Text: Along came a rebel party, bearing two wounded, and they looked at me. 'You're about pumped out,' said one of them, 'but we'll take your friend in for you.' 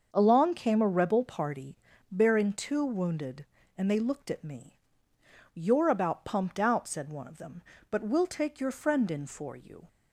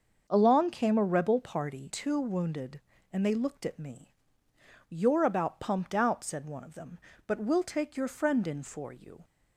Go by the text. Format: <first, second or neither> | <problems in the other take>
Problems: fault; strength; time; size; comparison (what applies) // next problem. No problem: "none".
first | starts louder than the rest; until 1.2 s; 6.5 dB; also in the first // skips "bearing"; at 1.9 s